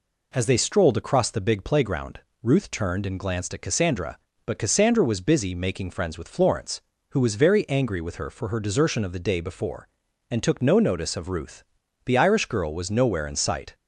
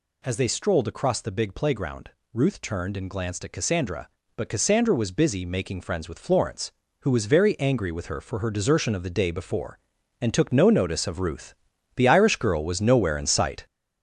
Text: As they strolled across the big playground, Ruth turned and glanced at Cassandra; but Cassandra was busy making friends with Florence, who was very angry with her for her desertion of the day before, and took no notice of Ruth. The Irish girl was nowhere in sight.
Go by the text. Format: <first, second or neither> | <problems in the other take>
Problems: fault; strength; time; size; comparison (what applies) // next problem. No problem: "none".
first | gets louder; noticeable; throughout; 6 dB